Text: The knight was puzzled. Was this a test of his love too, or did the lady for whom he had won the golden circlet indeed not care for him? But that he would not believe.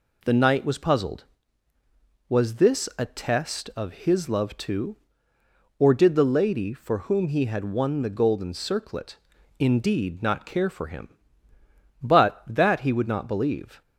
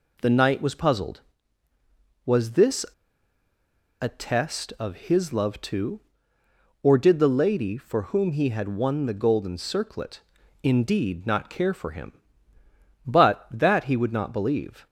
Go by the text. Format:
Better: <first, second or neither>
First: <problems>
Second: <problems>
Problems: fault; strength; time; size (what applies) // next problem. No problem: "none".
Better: first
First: pauses between "circlet" and "indeed"; at 9.1 s; 0.42 s long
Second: pauses between "this" and "a"; at 2.8 s; 1.1 s long // pauses between "circlet" and "indeed"; at 10.2 s; 0.42 s long